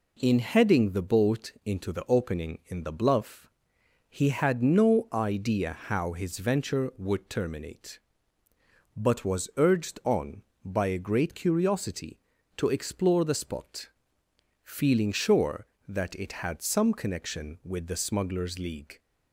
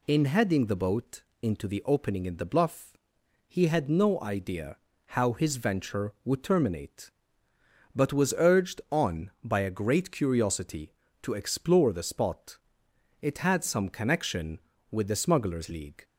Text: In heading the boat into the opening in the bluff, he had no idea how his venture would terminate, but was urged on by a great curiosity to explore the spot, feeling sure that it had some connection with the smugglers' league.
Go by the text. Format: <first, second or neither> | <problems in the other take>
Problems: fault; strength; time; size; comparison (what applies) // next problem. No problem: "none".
first | pauses between "boat" and "into"; slight; at 1.2 s; 0.18 s long // pauses between "idea" and "how"; slight; at 4.7 s; 0.30 s long // skips "feeling sure that"; at 12.8 s